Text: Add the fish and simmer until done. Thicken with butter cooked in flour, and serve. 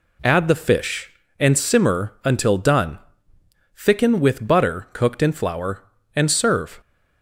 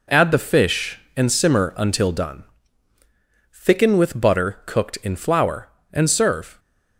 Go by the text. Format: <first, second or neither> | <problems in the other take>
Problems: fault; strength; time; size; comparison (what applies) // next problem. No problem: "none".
neither | none